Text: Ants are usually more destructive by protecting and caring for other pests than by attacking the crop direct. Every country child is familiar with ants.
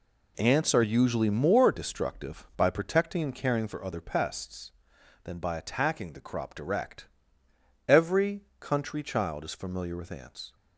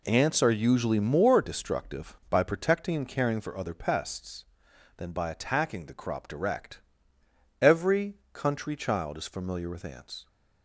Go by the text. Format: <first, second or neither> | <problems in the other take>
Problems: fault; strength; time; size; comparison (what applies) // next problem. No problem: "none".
neither | pauses between "Every" and "country"; slight; the same in both